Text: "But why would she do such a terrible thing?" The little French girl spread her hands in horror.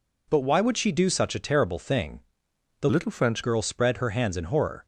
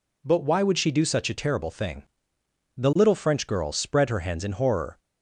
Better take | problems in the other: second | changes voice from "little" to "French"; from 2.8 to 3.4 s; 0.6 s long

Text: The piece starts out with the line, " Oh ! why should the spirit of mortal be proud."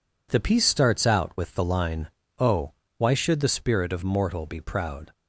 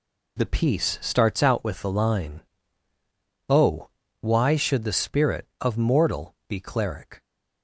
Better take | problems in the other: first | says "cleric" for "proud"; at 6.5 s

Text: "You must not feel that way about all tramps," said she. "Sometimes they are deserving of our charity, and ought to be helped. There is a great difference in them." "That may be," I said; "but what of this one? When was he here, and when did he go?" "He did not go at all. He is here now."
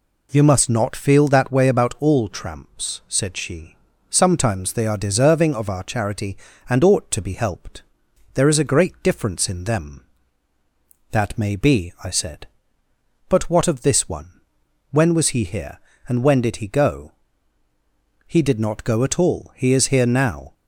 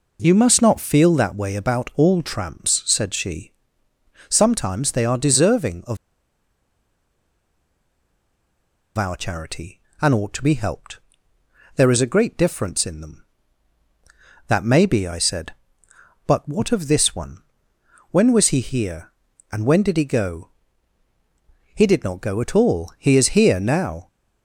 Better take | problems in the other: first | pauses between "of" and "our"; strong; at 5.9 s; 2.9 s long

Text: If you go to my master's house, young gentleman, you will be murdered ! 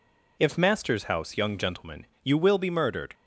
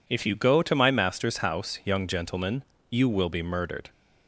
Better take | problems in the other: second | skips "you go to my"; at 0.5 s

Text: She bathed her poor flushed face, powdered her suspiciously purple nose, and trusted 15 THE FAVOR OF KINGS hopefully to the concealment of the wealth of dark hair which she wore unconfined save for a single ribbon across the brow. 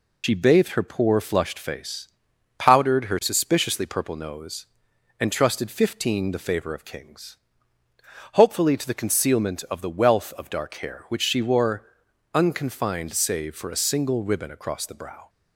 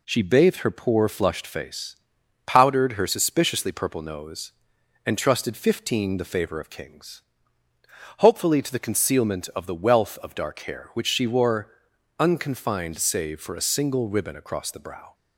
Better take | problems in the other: second | loses the start of "She"; at 0.2 s; 70 ms // pauses between "KINGS" and "hopefully"; noticeable; at 7.3 s; 0.96 s long; noticeable in the second // pauses between "wore" and "unconfined"; noticeable; at 11.8 s; 0.50 s long; noticeable in the second

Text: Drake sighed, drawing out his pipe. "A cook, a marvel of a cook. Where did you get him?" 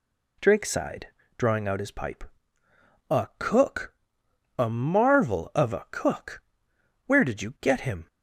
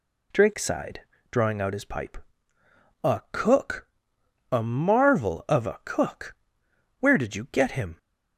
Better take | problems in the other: neither | none

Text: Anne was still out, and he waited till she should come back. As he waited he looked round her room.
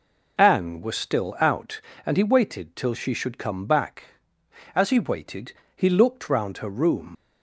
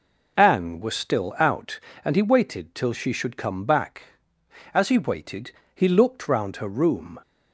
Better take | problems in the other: second | pauses between "waited" and "he"; slight; at 5.5 s; 0.24 s long; slight in the second // leaves "room" unfinished; at 7.1 s; 75 ms

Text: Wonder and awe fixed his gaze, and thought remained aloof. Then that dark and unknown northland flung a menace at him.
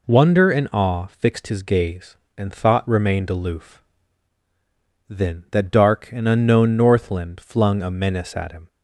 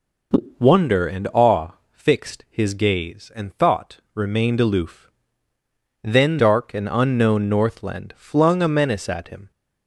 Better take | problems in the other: first | pauses between "awe" and "fixed"; slight; at 1.7 s; 0.20 s long // pauses between "thought" and "remained"; slight; at 3.9 s; 0.16 s long // skips "that"; at 6.3 s

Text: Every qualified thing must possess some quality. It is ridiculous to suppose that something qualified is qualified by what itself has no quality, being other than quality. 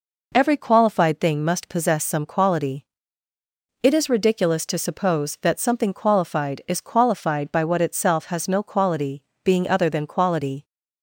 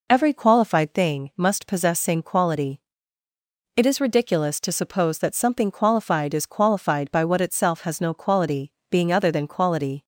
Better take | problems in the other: first | says "same" for "some"; at 1.9 s

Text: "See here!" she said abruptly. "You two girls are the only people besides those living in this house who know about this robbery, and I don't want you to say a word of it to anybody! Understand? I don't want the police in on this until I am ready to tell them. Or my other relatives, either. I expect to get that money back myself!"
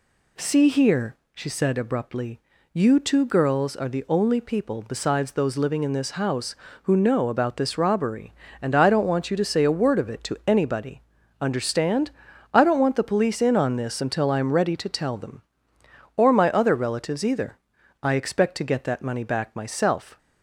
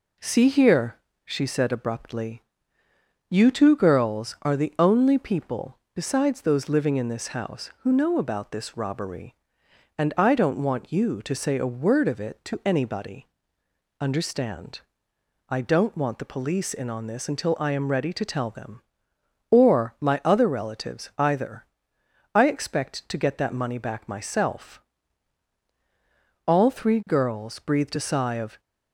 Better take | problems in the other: first | pauses between "people" and "besides"; slight; at 5.7 s; 0.16 s long // goes on to say "All three girls breathed a sigh of"; strong; from 26.4 s on; 2.1 s long

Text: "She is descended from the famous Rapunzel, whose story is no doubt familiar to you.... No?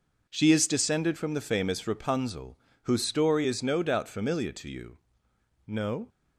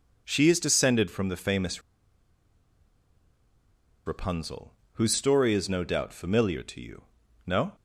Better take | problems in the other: first | pauses between "famous" and "Rapunzel"; strong; at 1.8 s; 2.2 s long

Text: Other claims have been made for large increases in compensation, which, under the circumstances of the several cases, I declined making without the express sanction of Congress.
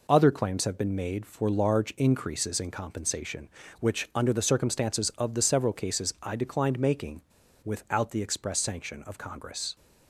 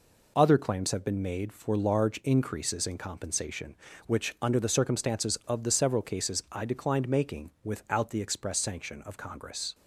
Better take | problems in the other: second | pauses between "making" and "without"; at 7.2 s; 0.41 s long

